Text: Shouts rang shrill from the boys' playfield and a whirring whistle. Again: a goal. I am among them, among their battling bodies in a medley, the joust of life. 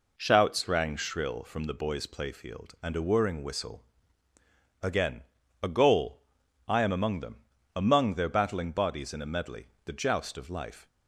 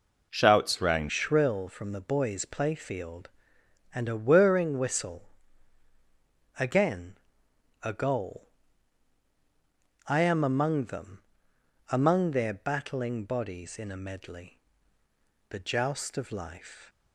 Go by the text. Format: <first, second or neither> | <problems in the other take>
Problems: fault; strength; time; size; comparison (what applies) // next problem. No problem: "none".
first | changes voice at "shrill"; from 1.0 s on; 15.8 s long